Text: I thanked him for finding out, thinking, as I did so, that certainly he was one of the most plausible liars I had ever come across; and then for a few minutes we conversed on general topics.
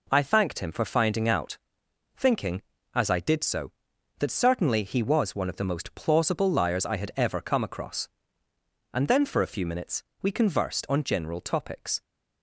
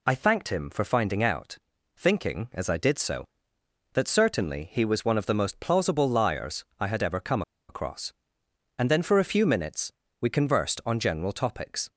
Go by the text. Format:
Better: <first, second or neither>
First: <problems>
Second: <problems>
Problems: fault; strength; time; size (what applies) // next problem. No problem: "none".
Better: first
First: pauses between "minutes" and "we"; slight; at 10.0 s; 0.18 s long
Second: pauses between "come" and "across"; slight; at 7.4 s; 0.27 s long // pauses between "minutes" and "we"; slight; at 9.9 s; 0.28 s long